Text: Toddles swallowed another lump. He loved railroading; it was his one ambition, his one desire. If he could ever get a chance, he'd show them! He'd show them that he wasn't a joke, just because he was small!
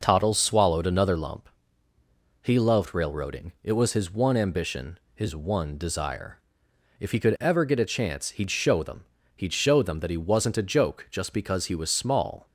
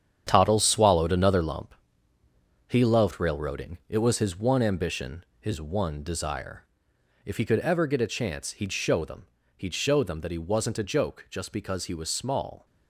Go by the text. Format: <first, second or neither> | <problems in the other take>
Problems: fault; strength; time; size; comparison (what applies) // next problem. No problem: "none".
first | gets quieter; strong; throughout; 9 dB